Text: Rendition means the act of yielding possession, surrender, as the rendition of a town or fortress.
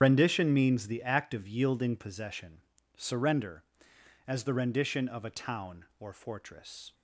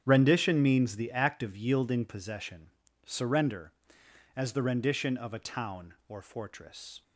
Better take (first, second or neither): second